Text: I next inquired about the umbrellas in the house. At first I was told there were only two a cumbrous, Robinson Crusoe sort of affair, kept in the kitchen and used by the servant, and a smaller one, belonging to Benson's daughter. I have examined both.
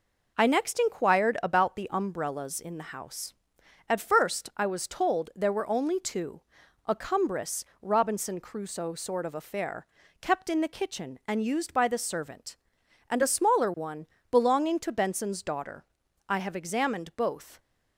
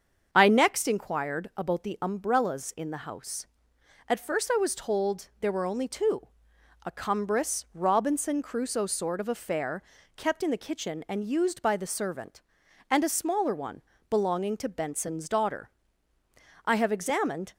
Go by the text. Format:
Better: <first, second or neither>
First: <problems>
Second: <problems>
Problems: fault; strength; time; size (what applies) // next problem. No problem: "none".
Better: first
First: pauses between "two" and "a"; at 6.4 s; 0.44 s long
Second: starts louder than the rest; until 1.3 s; 7 dB // pauses between "two" and "a"; noticeable; at 6.2 s; 0.60 s long // stops before "both"; at 17.5 s